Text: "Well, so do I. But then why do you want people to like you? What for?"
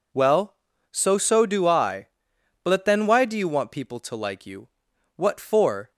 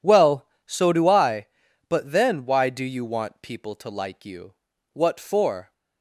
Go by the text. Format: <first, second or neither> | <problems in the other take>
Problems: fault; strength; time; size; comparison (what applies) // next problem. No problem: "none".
second | says "so" twice; at 1.1 s